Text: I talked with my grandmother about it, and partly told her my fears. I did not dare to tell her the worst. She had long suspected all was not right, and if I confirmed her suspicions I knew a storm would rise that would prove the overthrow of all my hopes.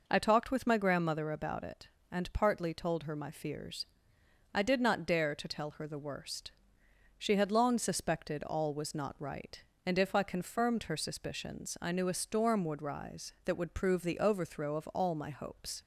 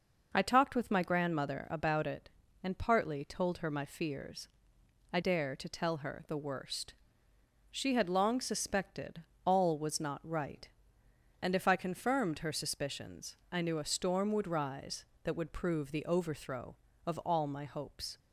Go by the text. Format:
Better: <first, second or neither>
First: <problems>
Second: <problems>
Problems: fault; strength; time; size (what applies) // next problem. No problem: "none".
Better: first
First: none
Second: skips "did not"; at 5.2 s // pauses between "suspected" and "all"; slight; at 9.2 s; 0.22 s long // pauses between "suspicions" and "I"; slight; at 13.3 s; 0.16 s long